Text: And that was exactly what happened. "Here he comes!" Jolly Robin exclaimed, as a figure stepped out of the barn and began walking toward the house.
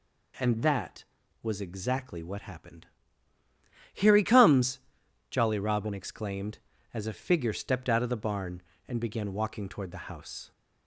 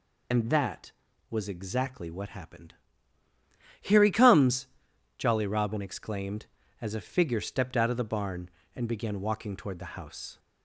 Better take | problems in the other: first | loses the start of "And"; at 0.3 s; 90 ms

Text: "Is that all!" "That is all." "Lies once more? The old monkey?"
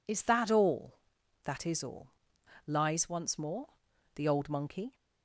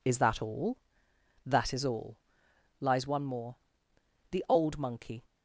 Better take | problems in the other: first | says "one" for "once"; at 3.0 s

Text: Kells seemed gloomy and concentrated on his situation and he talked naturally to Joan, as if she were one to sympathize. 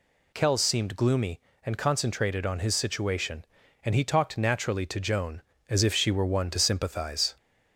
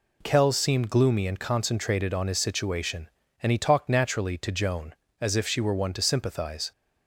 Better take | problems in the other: neither | none

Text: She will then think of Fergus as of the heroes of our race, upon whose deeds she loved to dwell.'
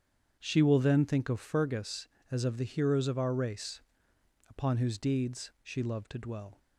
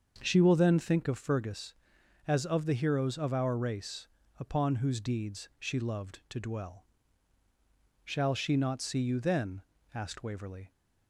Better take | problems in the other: first | starts louder than the rest; until 1.2 s; 6.5 dB; strong in the first // goes on to say "Shall she not see you then asked Waverley"; strong; from 8.0 s on; 2.6 s long

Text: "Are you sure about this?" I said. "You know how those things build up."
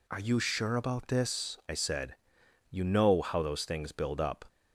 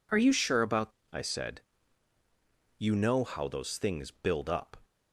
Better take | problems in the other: first | skips "this"; at 1.0 s

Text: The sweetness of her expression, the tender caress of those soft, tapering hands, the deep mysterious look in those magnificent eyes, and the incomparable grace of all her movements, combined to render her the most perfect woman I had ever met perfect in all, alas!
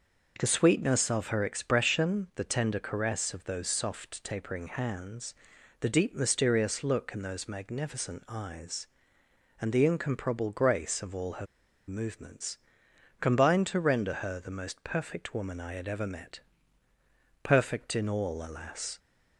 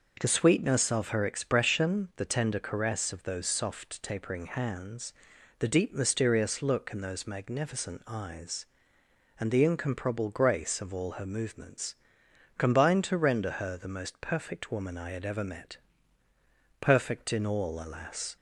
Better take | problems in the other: second | pauses between "her" and "movements"; at 11.4 s; 0.42 s long // pauses between "met" and "perfect"; at 16.4 s; 1.0 s long; also in the second

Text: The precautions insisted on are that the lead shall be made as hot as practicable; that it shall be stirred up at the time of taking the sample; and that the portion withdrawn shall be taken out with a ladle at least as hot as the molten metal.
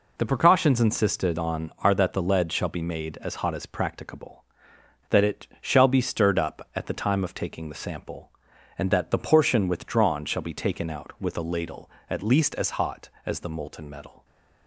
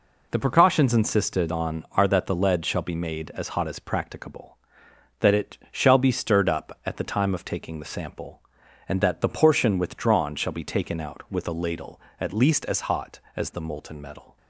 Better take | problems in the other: neither | none

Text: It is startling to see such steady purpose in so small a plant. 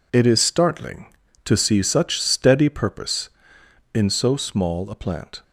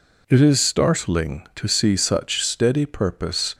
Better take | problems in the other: first | stops before "in so small a plant"; at 3.5 s

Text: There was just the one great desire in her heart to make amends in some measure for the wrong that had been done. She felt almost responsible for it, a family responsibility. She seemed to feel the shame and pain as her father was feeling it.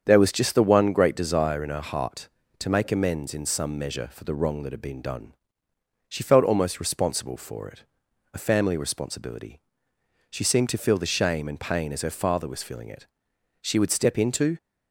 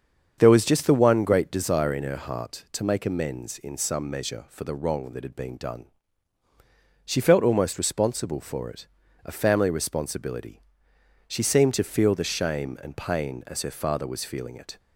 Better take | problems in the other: second | starts louder than the rest; strong; until 1.0 s; 7.5 dB; strong in the second // goes on to say "She would step into"; noticeable; from 13.6 s on; 0.94 s long

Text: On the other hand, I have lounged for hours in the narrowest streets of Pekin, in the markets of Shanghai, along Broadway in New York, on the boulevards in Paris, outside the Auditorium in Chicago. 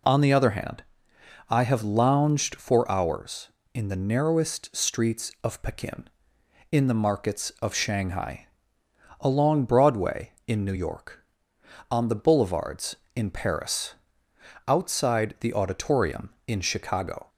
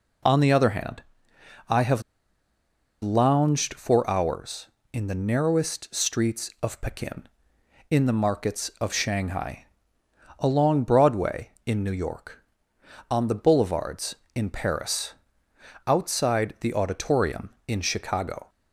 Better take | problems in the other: first | pauses between "have" and "lounged"; at 2.0 s; 1.0 s long

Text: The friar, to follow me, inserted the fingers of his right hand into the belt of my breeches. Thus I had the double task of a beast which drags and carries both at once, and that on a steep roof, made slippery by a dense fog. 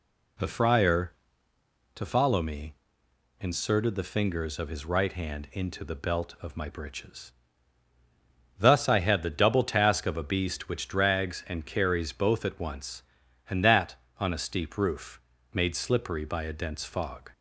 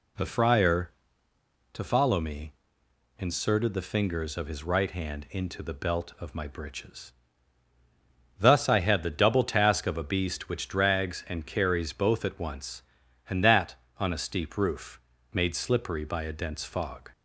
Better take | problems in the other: neither | none

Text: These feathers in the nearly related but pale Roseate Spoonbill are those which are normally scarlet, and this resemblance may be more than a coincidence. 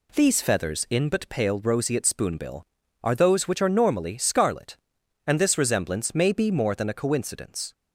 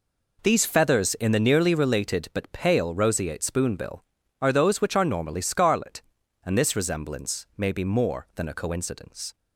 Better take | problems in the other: second | skips "the nearly related"; at 1.0 s

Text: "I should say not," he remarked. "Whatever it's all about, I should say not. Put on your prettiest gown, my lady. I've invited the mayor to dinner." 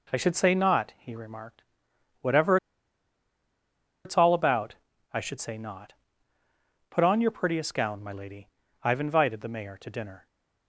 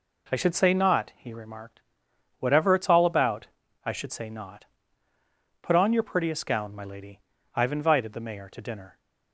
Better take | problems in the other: second | pauses between "Whatever" and "it's"; strong; at 2.5 s; 1.4 s long

